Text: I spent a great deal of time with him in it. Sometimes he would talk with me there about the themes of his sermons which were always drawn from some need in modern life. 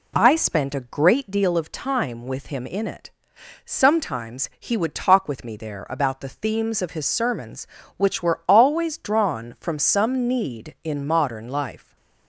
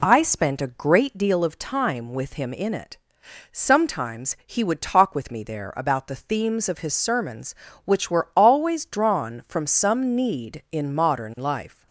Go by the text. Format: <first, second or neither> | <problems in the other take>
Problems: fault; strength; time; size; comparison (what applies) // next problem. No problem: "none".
neither | none